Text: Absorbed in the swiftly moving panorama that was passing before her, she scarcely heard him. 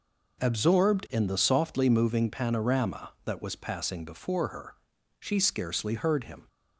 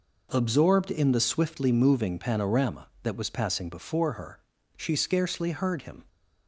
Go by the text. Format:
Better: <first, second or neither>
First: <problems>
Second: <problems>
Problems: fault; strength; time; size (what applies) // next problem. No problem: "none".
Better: second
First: says "softly" for "swiftly"; at 1.3 s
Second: none